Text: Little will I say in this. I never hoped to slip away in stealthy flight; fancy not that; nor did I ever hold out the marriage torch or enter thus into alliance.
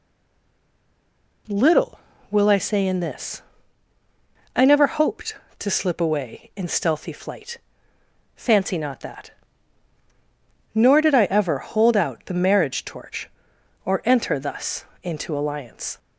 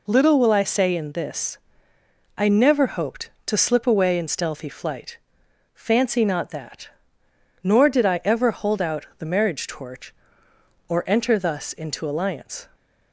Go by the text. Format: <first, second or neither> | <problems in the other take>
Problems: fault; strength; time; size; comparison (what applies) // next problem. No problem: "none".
second | stays silent before the first word; noticeable; until 1.4 s; 1.4 s long // pauses between "thus" and "into"; slight; at 14.8 s; 0.18 s long